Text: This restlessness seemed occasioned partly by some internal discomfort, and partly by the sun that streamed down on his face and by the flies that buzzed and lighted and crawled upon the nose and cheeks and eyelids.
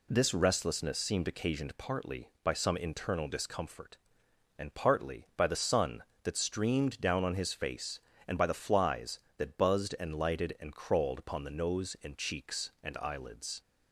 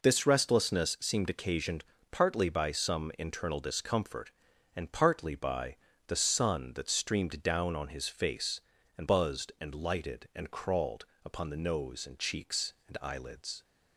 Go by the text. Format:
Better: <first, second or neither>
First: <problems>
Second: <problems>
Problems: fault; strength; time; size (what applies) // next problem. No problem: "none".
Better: first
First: none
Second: pauses between "occasioned" and "partly"; slight; at 1.8 s; 0.30 s long // pauses between "by" and "the"; slight; at 5.7 s; 0.32 s long // skips "by the flies that"; at 9.0 s // pauses between "crawled" and "upon"; slight; at 11.0 s; 0.18 s long